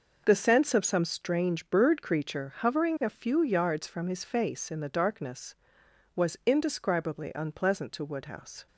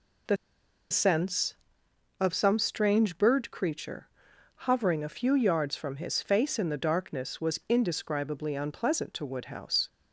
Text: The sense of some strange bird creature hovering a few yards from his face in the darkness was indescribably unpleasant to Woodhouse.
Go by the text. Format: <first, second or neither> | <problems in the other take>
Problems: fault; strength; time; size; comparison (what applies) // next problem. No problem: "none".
first | pauses between "The" and "sense"; noticeable; at 0.3 s; 0.55 s long // pauses between "creature" and "hovering"; noticeable; at 4.0 s; 0.58 s long